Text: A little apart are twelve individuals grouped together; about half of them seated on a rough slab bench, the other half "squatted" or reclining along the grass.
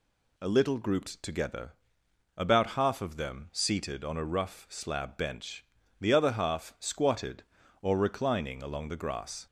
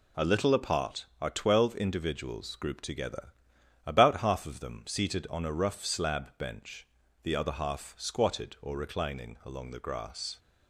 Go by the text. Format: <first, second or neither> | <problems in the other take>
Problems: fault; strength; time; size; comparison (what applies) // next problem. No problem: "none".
second | skips "apart are twelve individuals"; at 0.7 s